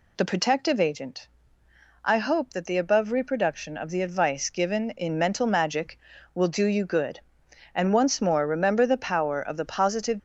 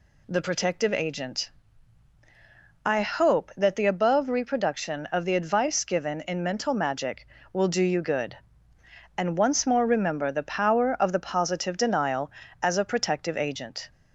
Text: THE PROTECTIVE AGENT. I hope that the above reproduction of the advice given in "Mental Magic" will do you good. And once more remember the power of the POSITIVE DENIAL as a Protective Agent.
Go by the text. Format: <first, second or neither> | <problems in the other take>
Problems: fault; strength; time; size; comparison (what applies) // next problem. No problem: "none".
second | stops before "DENIAL as a Protective Agent"; at 10.1 s